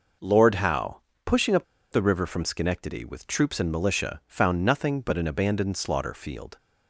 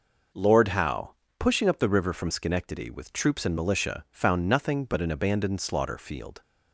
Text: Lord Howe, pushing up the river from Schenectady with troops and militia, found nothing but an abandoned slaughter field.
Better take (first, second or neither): second